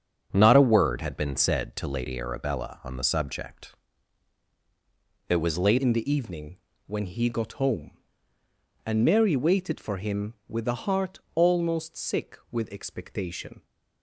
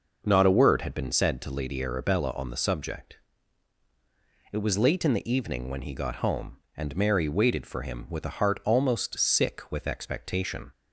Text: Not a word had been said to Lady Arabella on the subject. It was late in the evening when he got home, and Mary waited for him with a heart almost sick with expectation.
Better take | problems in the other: second | starts louder than the rest; until 1.3 s; 7 dB // changes voice at "in"; from 5.7 s on; 7.9 s long // pauses between "evening" and "when"; slight; at 6.5 s; 0.28 s long // pauses between "heart" and "almost"; slight; at 11.1 s; 0.16 s long

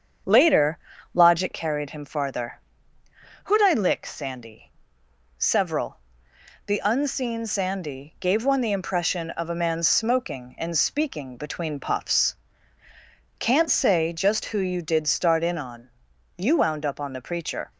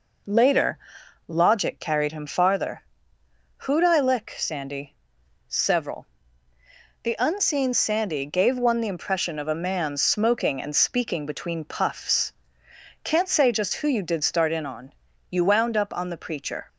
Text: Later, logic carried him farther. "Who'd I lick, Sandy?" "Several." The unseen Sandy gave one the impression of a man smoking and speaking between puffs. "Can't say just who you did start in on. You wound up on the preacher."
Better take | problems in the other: second | starts louder than the rest; strong; until 1.7 s; 7 dB

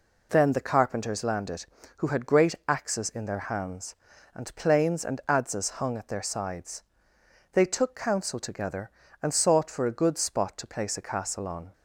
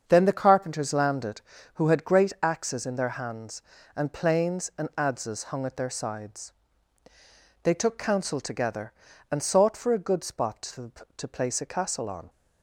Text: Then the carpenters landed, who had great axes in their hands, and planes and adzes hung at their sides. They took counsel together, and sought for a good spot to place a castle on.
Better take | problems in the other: first | starts louder than the rest; until 1.0 s; 7 dB // says "to" twice; at 11.1 s

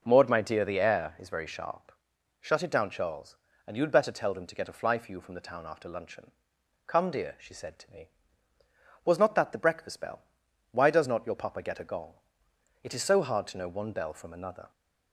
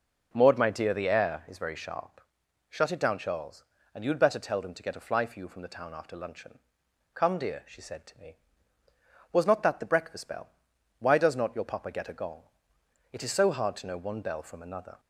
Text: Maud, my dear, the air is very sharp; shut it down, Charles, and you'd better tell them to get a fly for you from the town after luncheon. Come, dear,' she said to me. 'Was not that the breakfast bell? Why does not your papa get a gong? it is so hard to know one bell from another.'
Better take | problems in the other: neither | none

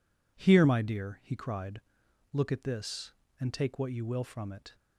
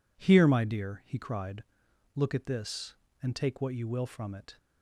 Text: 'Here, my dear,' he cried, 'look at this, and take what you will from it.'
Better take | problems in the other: neither | none

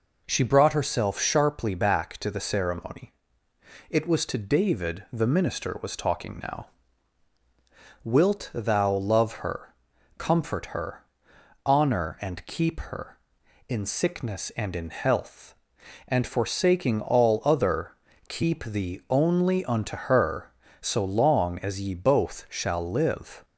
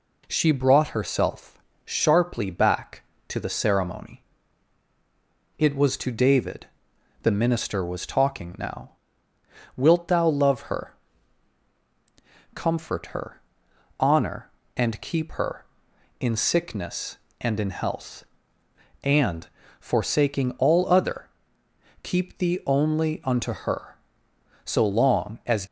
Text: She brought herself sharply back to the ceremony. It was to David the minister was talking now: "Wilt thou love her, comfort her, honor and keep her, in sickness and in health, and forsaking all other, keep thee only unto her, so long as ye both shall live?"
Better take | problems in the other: first | pauses between "herself" and "sharply"; slight; at 1.5 s; 0.26 s long // pauses between "David" and "the"; noticeable; at 6.6 s; 0.56 s long // pauses between "and" and "forsaking"; slight; at 19.4 s; 0.30 s long // stops before "ye both shall live"; at 25.6 s

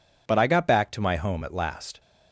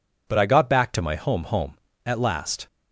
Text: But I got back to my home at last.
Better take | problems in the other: first | says "home" twice; at 1.4 s

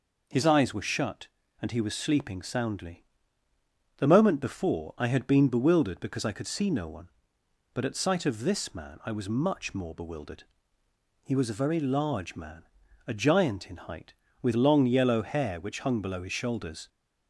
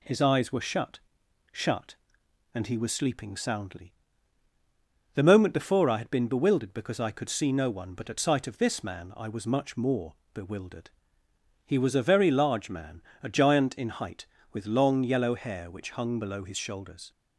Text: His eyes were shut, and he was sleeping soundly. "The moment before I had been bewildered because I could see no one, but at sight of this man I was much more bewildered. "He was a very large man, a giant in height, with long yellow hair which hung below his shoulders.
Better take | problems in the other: first | says "shut" twice; at 1.5 s // pauses between "more" and "bewildered"; slight; at 10.1 s; 0.18 s long

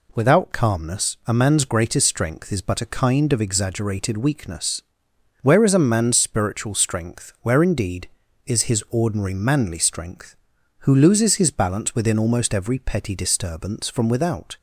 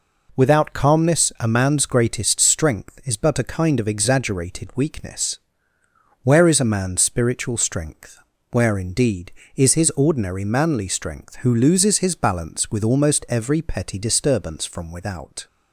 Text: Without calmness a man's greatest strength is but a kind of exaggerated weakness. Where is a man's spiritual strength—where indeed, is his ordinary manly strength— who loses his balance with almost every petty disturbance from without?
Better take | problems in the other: second | says "within" for "with"; at 11.9 s

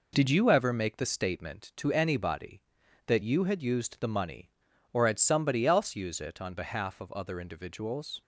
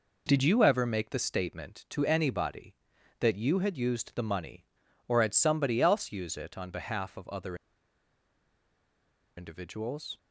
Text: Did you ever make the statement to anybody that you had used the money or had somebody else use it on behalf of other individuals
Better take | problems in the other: first | pauses between "other" and "individuals"; strong; at 7.5 s; 1.8 s long

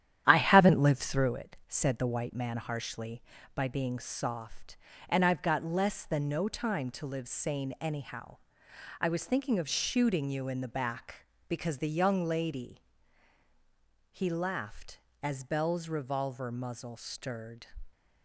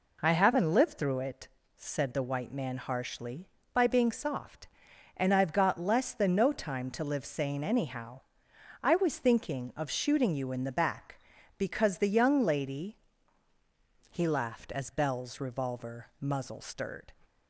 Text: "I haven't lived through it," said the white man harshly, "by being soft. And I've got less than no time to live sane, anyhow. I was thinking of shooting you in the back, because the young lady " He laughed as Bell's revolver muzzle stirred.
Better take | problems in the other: second | starts louder than the rest; strong; until 1.3 s; 11 dB

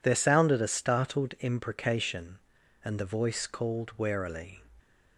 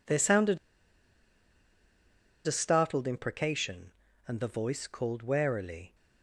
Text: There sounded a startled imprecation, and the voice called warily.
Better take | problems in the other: first | pauses between "sounded" and "a"; strong; at 0.5 s; 1.8 s long

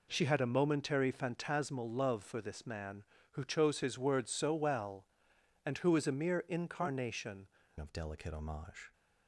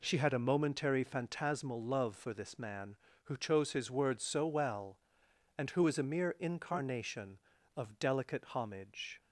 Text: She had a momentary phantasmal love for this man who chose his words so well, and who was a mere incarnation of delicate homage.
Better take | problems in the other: second | changes voice at "of"; from 7.8 s on; 1.1 s long

